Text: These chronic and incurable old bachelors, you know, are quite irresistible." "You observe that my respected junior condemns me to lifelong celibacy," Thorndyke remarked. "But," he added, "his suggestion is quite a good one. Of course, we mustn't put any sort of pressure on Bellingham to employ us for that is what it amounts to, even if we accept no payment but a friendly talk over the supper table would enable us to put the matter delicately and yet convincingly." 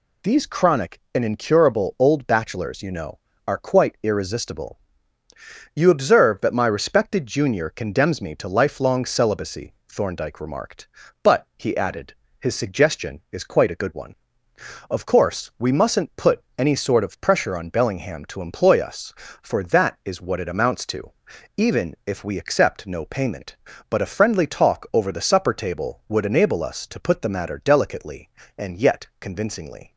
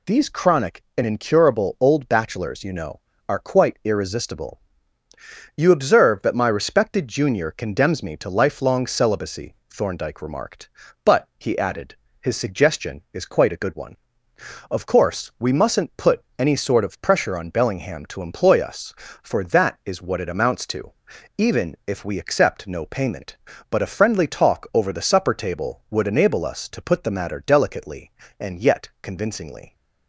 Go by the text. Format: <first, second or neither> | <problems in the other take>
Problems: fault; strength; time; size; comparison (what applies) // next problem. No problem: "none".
neither | none